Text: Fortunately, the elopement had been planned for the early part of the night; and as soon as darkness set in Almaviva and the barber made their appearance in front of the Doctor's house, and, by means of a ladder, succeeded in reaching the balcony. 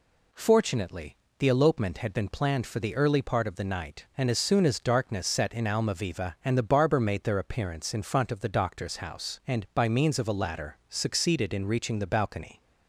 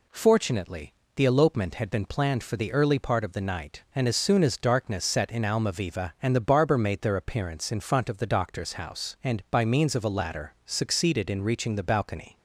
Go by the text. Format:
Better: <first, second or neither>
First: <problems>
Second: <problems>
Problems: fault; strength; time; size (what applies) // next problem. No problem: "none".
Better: neither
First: none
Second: none